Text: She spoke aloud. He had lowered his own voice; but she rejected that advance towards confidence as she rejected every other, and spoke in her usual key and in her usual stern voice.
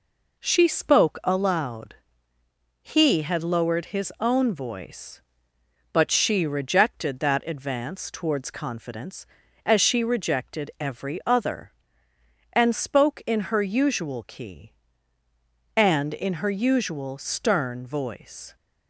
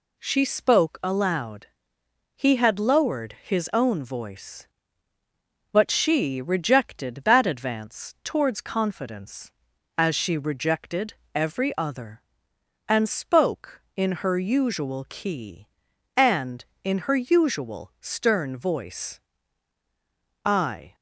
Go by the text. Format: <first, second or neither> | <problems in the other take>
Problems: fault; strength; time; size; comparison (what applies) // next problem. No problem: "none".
first | pauses between "rejected" and "every"; slight; at 11.1 s; 0.20 s long // goes on to say "I"; from 20.4 s on; 0.50 s long